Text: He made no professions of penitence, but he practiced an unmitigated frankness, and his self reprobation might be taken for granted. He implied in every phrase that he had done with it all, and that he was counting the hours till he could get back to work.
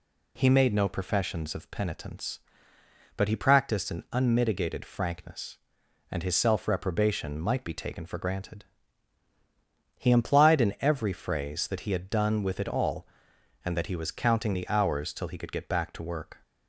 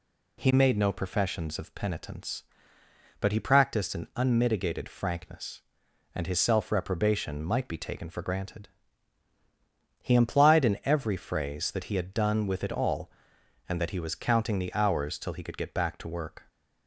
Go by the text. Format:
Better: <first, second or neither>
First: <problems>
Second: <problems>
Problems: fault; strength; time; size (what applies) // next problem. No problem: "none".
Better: neither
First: none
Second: none